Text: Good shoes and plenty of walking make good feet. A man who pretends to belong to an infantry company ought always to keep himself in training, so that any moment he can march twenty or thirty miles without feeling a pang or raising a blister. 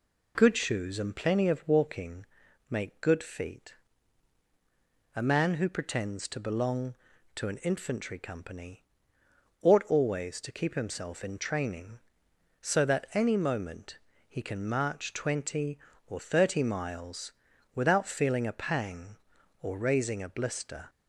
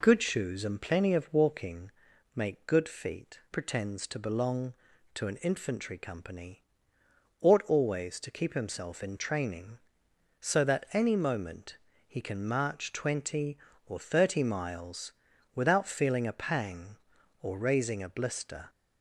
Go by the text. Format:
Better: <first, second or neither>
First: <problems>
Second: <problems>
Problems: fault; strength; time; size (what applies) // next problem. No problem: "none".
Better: first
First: pauses between "walking" and "make"; at 2.2 s; 0.42 s long // pauses between "company" and "ought"; noticeable; at 8.8 s; 0.80 s long // pauses between "moment" and "he"; slight; at 13.9 s; 0.32 s long // pauses between "miles" and "without"; at 17.3 s; 0.42 s long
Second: pauses between "walking" and "make"; at 1.9 s; 0.42 s long // skips "A man who"; at 3.4 s // pauses between "company" and "ought"; noticeable; at 6.6 s; 0.80 s long // pauses between "moment" and "he"; slight; at 11.7 s; 0.32 s long // pauses between "miles" and "without"; at 15.1 s; 0.42 s long